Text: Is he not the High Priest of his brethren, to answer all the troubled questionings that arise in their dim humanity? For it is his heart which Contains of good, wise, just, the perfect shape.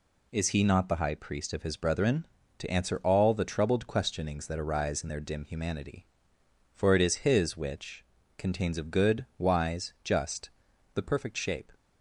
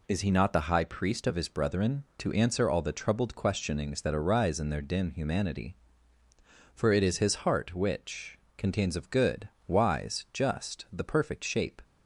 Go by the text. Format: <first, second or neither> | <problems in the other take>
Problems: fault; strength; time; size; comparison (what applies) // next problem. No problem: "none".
second | skips "heart"; at 7.5 s // pauses between "which" and "Contains"; slight; at 8.0 s; 0.34 s long; slight in the second